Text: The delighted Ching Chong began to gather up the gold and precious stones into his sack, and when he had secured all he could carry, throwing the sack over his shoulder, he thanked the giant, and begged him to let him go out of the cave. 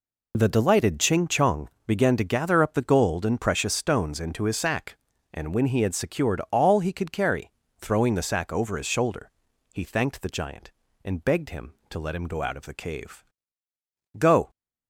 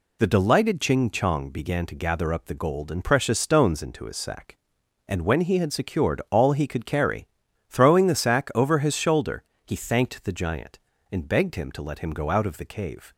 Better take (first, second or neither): second